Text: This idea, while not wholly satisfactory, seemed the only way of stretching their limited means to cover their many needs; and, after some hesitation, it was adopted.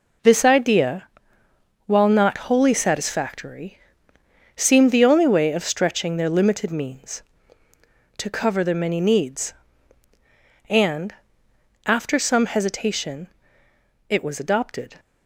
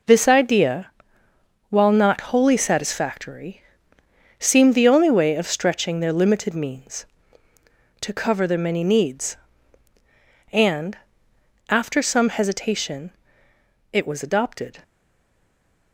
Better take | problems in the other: first | stays silent after the last word; from 14.8 s on; 1.1 s long

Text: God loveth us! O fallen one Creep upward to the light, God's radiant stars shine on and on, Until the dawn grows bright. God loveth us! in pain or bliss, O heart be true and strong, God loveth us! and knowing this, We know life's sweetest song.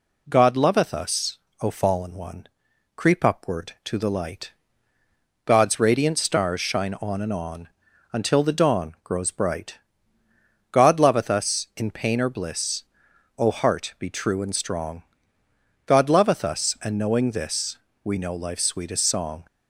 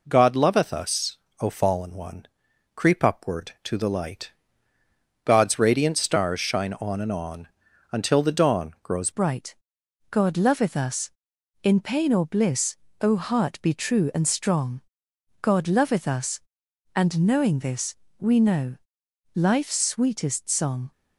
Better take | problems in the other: first | pauses between "one" and "Creep"; noticeable; at 2.2 s; 0.48 s long; noticeable in the first // changes voice at "bright"; from 9.1 s on; 11.8 s long // pauses between "know" and "life's"; noticeable; at 18.7 s; 0.56 s long

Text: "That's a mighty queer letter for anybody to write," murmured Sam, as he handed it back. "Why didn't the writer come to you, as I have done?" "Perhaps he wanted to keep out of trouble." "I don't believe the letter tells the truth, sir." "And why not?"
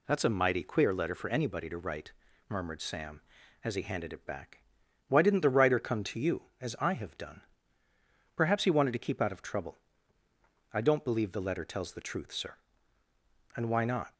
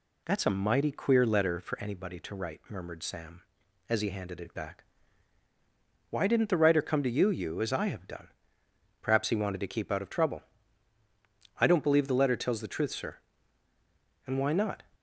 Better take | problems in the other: first | says "you" twice; at 7.3 s

